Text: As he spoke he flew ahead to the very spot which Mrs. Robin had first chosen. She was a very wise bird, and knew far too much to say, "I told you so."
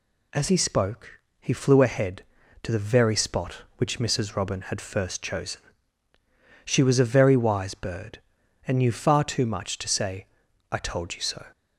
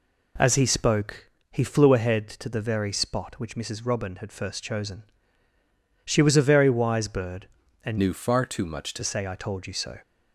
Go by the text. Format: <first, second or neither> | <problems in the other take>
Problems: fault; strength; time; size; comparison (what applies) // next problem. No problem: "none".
first | pauses between "spoke" and "he"; slight; at 1.3 s; 0.20 s long; slight in the first // changes voice from "knew" to "to"; from 7.9 to 9.0 s; 1.1 s long